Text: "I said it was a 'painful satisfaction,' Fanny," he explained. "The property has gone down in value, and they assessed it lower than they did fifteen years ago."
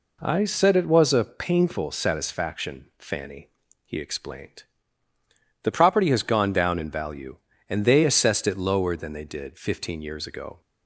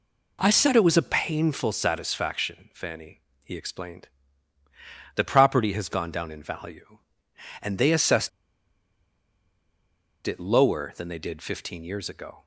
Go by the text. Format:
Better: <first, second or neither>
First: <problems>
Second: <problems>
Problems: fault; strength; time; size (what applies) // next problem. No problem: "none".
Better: first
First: none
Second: pauses between "assessed" and "it"; strong; at 8.2 s; 1.9 s long